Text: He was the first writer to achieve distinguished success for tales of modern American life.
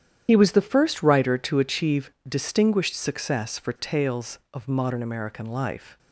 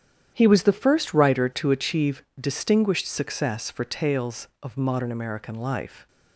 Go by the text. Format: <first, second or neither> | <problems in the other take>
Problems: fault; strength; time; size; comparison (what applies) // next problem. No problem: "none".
second | loses the start of "He"; at 0.2 s; 55 ms // starts louder than the rest; strong; until 1.2 s; 10 dB; strong in the second // pauses between "achieve" and "distinguished"; slight; at 2.0 s; 0.16 s long; slight in the second